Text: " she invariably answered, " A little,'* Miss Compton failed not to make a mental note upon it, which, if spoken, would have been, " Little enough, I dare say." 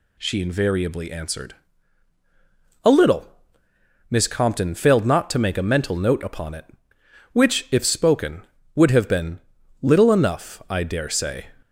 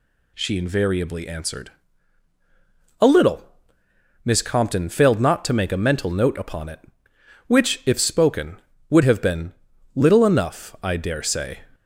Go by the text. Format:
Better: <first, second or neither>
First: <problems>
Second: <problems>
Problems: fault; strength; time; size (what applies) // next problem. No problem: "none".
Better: neither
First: none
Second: none